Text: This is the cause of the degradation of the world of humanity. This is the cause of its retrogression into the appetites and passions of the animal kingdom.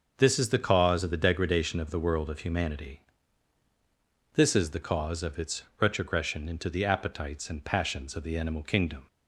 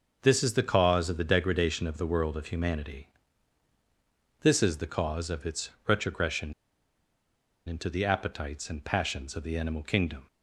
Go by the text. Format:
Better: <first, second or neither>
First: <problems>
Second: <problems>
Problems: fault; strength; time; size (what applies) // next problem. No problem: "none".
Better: first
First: starts louder than the rest; until 1.2 s; 6.5 dB // pauses between "its" and "retrogression"; slight; at 5.6 s; 0.18 s long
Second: starts louder than the rest; until 1.2 s; 6 dB // pauses between "its" and "retrogression"; slight; at 5.6 s; 0.18 s long // pauses between "retrogression" and "into"; at 6.5 s; 1.1 s long